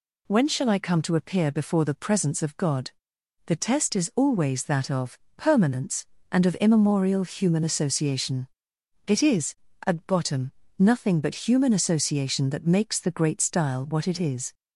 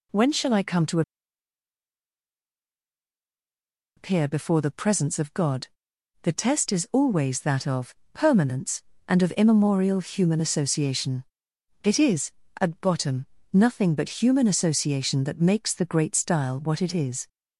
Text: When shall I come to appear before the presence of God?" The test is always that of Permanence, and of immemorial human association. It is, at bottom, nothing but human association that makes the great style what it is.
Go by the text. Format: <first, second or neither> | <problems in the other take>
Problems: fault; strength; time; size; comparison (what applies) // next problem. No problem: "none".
first | pauses between "to" and "appear"; strong; at 1.0 s; 2.9 s long // pauses between "of" and "Permanence"; slight; at 7.9 s; 0.18 s long; slight in the first